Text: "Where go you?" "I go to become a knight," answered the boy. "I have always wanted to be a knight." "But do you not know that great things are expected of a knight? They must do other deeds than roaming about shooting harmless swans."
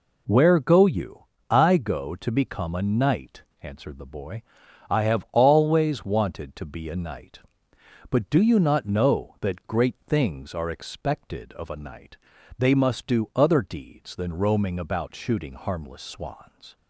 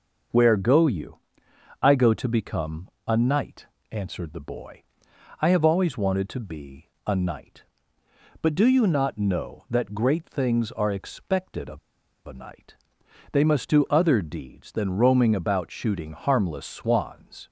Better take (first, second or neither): first